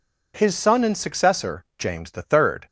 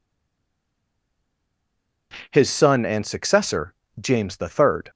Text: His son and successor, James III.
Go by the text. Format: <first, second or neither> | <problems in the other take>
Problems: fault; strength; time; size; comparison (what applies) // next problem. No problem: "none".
first | stays silent before the first word; noticeable; until 2.1 s; 2.1 s long